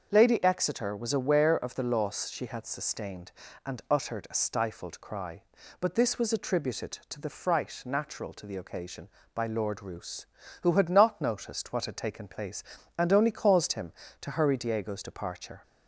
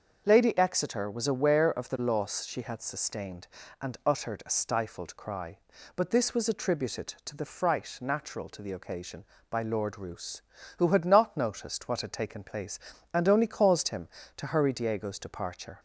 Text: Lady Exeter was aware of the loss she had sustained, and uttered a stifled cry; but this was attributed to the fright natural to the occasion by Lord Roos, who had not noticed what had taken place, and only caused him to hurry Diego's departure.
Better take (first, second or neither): neither